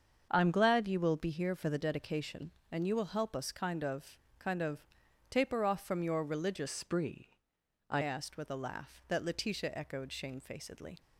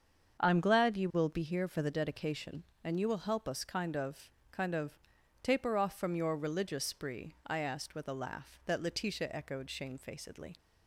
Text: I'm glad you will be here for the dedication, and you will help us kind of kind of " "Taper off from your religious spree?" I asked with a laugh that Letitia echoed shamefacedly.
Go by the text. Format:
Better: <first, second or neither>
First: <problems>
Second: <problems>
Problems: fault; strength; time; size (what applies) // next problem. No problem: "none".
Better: second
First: starts louder than the rest; until 1.3 s; 7 dB // pauses between "of" and "kind"; slight; at 4.1 s; 0.22 s long // changes voice from "spree" to "I"; from 6.6 to 8.0 s; 1.4 s long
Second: starts louder than the rest; until 1.4 s; 7 dB // pauses between "of" and "kind"; slight; at 4.2 s; 0.22 s long